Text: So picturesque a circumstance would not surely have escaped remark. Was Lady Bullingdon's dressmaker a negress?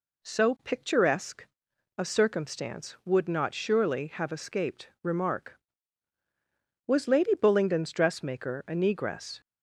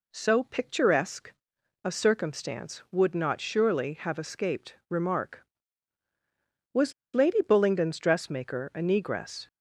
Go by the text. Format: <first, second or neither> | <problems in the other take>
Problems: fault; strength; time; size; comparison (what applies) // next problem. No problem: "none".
first | pauses between "picturesque" and "a"; noticeable; at 1.3 s; 0.52 s long; noticeable in the first // pauses between "Was" and "Lady"; slight; at 6.9 s; 0.22 s long